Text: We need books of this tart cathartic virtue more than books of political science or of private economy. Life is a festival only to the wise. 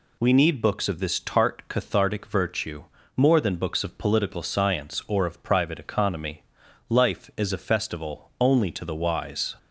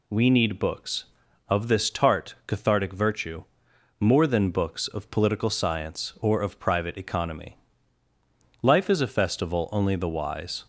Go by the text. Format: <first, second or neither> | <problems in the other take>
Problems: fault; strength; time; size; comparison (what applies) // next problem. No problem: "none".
first | pauses between "virtue" and "more"; noticeable; at 3.4 s; 0.56 s long; slight in the first // skips "to"; at 9.9 s